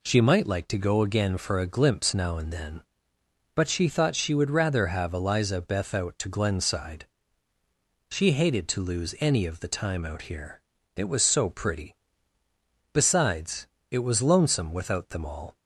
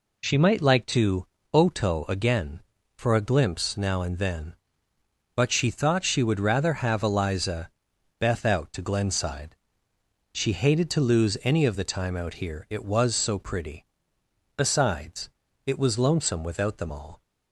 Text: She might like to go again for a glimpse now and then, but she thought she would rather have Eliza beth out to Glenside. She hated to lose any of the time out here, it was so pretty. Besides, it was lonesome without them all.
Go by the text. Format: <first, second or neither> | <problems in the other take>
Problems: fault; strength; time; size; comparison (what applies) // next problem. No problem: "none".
first | says "oto" for "go"; at 1.5 s // pauses between "Eliza" and "beth"; noticeable; at 7.7 s; 0.48 s long